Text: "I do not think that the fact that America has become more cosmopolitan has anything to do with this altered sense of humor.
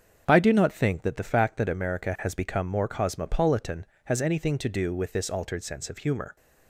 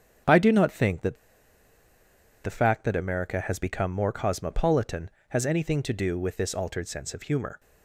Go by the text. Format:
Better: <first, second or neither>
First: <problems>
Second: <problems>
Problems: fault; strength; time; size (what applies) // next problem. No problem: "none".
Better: first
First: starts louder than the rest; until 1.2 s; 7 dB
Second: starts louder than the rest; strong; until 2.5 s; 7 dB // pauses between "that" and "the"; strong; at 1.1 s; 1.2 s long